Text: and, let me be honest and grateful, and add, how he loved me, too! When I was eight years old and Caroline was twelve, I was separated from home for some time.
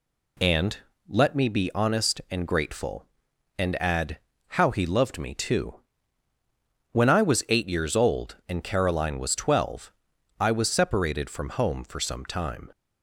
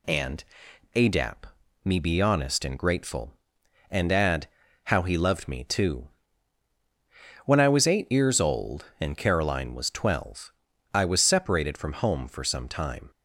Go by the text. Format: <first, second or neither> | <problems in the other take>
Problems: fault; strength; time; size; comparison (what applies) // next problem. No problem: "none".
first | says "adap" for "let"; at 0.9 s